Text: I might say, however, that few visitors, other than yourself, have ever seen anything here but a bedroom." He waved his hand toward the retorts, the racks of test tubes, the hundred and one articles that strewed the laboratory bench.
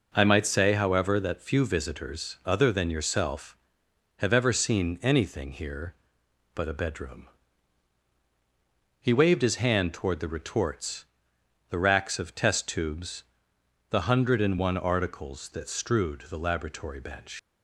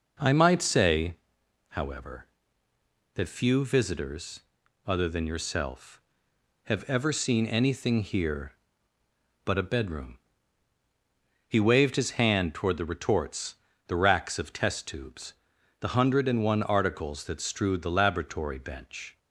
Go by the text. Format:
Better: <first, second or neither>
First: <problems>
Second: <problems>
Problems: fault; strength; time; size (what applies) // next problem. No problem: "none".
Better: second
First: leaves "bench" unfinished; at 17.3 s; 105 ms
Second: none